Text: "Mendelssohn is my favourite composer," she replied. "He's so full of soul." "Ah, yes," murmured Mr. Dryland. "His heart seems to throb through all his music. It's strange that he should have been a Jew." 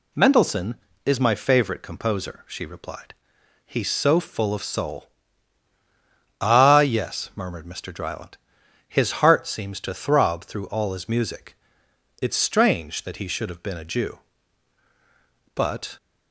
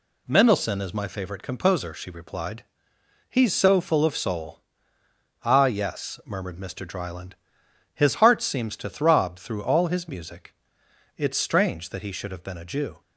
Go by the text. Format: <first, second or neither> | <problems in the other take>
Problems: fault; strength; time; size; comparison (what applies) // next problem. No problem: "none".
second | goes on to say "But"; slight; from 15.5 s on; 0.42 s long